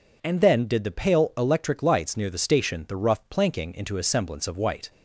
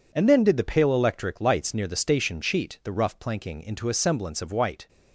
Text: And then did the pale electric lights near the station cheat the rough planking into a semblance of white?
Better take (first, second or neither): second